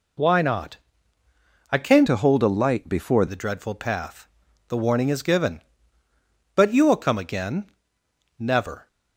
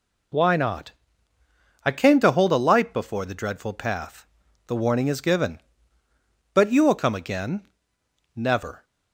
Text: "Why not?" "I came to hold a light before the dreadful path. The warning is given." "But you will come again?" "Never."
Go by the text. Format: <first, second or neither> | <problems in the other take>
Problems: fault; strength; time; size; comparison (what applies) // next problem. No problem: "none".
second | changes voice from "to" to "before"; from 2.0 to 3.2 s; 1.2 s long